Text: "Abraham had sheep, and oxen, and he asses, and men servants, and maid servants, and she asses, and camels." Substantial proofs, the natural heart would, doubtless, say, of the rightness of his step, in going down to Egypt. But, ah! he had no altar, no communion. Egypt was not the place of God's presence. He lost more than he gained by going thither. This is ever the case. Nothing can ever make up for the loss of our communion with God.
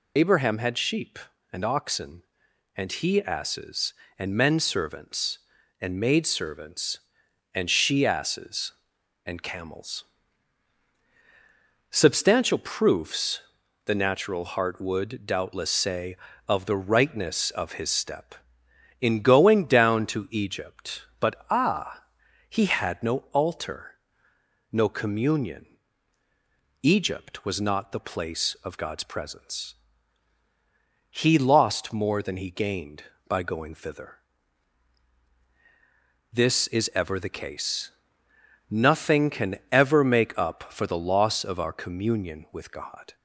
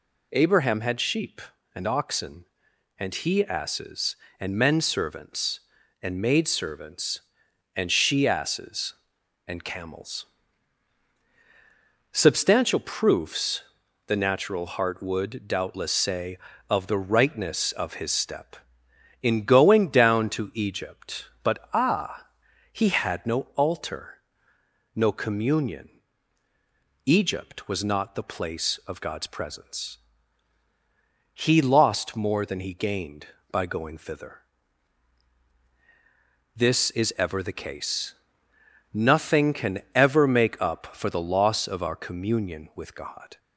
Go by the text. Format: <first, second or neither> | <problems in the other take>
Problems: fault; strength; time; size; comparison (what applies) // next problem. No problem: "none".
second | loses the start of "Abraham"; at 0.1 s; 65 ms // pauses between "no" and "altar"; slight; at 23.1 s; 0.16 s long; slight in the second